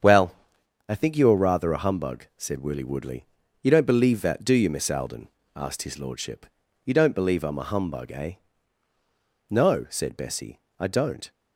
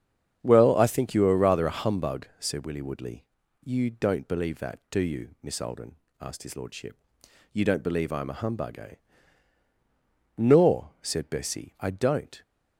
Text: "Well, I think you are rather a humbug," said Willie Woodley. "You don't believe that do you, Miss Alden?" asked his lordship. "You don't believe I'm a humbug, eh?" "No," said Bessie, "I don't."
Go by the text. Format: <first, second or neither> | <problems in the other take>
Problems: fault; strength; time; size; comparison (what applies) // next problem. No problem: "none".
first | starts louder than the rest; strong; until 1.4 s; 7.5 dB; strong in the first // says "Nor" for "No"; at 10.3 s